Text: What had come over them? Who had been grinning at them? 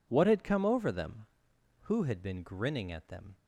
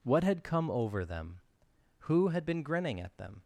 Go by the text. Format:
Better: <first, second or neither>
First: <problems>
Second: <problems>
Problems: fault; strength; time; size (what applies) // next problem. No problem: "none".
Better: neither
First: none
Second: none